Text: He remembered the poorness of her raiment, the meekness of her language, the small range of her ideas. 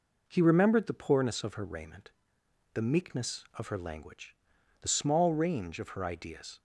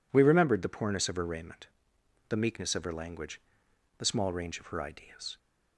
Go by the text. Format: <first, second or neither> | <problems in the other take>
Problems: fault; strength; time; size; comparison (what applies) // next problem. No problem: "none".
first | says "We" for "He"; at 0.1 s